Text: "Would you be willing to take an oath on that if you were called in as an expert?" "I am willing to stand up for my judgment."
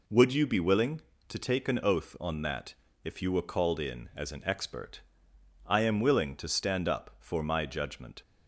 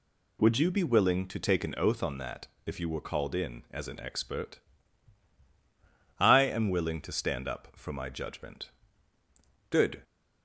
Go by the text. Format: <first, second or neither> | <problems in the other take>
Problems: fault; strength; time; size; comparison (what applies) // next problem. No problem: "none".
first | pauses between "that" and "if"; slight; at 2.4 s; 0.18 s long; slight in the first // goes on to say "Good"; slight; from 9.6 s on; 0.32 s long